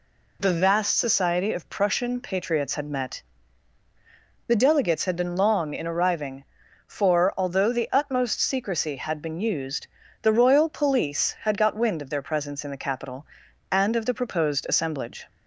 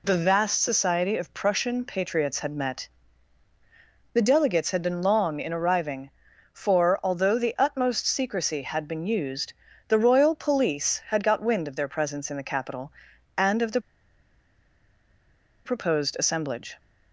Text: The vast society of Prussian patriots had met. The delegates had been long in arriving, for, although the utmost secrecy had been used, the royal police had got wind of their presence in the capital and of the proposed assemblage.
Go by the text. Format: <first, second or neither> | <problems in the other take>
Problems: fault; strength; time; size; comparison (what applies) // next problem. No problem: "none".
first | pauses between "the" and "proposed"; strong; at 13.8 s; 1.8 s long